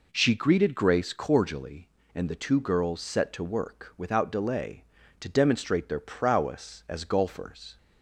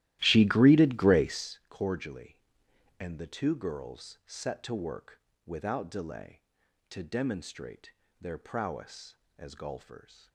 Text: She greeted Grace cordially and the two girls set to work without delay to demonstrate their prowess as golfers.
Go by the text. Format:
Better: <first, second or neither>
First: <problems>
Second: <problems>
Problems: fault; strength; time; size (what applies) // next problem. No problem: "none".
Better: first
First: none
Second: starts louder than the rest; strong; until 1.6 s; 15 dB // pauses between "work" and "without"; slight; at 5.1 s; 0.28 s long // pauses between "demonstrate" and "their"; slight; at 7.9 s; 0.28 s long